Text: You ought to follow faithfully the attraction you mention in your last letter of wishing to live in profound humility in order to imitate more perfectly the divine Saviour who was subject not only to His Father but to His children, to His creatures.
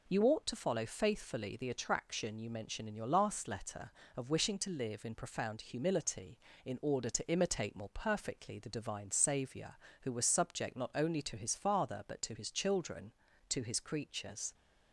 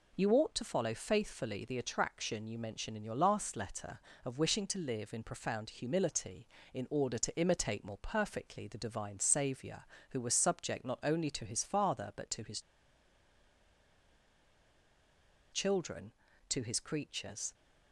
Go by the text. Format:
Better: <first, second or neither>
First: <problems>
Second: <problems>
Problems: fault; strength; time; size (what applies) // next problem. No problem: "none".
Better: first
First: none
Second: pauses between "His" and "children"; strong; at 12.5 s; 2.9 s long